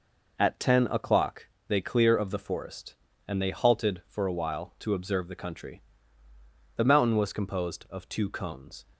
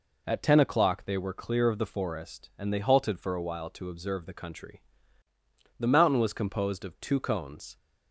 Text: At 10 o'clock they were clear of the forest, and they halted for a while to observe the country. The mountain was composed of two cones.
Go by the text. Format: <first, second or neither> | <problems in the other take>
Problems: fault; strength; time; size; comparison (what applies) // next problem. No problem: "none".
second | pauses between "o'clock" and "they"; slight; at 1.4 s; 0.22 s long // skips "were"; at 1.8 s